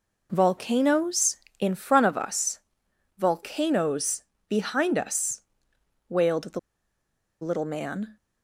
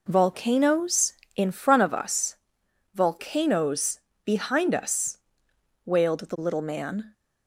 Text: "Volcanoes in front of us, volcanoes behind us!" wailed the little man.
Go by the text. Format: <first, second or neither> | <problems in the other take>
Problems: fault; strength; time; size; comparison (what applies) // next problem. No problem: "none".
second | pauses between "volcanoes" and "behind"; slight; at 4.2 s; 0.24 s long; slight in the second // pauses between "the" and "little"; noticeable; at 6.5 s; 0.82 s long